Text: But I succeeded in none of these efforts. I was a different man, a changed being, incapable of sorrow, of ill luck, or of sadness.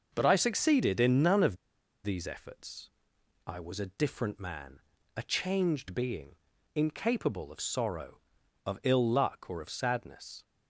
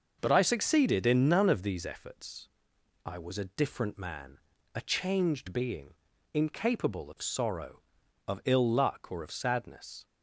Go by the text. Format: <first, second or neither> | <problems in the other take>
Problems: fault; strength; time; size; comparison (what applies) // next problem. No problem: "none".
second | starts louder than the rest; noticeable; until 1.1 s; 6 dB; noticeable in the second // pauses between "of" and "these"; noticeable; at 1.5 s; 0.47 s long